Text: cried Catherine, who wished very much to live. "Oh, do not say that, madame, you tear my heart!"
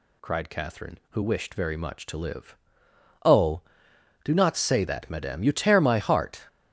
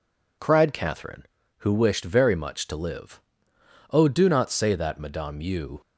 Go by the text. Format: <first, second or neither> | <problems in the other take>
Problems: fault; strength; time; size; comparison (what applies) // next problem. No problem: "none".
first | stops before "tear my heart"; at 5.8 s